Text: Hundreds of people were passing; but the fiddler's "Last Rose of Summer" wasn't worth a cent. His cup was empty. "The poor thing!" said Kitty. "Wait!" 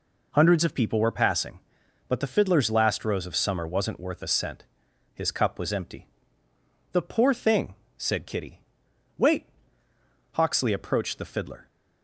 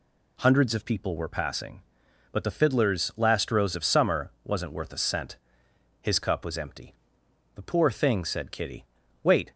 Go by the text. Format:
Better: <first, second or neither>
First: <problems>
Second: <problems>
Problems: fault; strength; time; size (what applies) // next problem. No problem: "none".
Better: second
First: goes on to say "Hawksley approached the fiddler"; noticeable; from 10.3 s on; 1.2 s long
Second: none